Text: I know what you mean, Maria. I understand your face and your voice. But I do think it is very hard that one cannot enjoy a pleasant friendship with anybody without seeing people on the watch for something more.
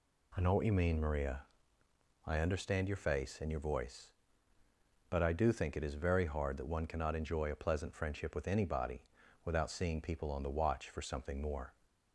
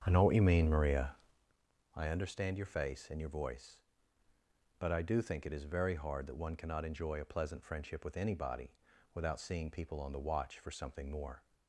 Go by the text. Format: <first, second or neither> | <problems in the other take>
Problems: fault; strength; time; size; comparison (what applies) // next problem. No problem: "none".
first | starts louder than the rest; strong; until 1.5 s; 8 dB // pauses between "anybody" and "without"; at 8.7 s; 0.42 s long; also in the first